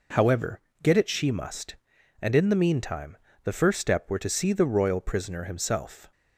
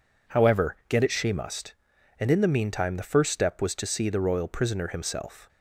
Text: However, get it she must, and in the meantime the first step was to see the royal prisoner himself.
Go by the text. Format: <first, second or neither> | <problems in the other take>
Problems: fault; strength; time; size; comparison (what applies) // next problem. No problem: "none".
second | pauses between "meantime" and "the"; slight; at 3.1 s; 0.30 s long // says "were" for "was"; at 4.0 s